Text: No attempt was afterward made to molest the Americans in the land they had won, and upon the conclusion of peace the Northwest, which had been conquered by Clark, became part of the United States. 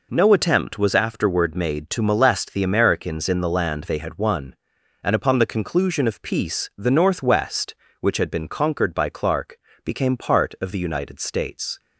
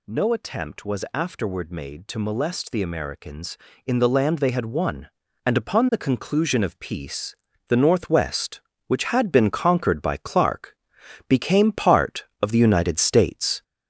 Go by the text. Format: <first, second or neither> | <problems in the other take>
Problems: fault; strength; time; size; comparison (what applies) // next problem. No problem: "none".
first | gets louder; noticeable; throughout; 4.5 dB // pauses between "peace" and "the"; slight; at 7.3 s; 0.34 s long